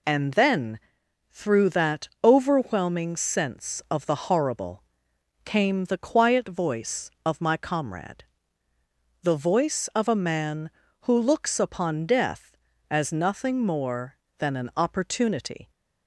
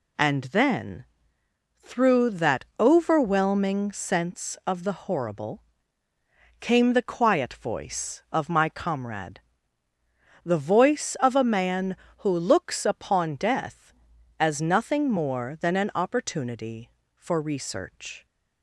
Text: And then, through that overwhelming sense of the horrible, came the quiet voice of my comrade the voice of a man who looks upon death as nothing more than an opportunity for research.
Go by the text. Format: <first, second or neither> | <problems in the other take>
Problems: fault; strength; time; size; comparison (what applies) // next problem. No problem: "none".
second | pauses between "comrade" and "the"; at 8.2 s; 1.0 s long; also in the second // stops before "for research"; at 15.6 s